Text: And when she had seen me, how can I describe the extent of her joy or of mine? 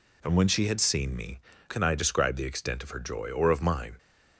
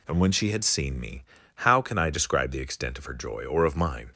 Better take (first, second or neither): second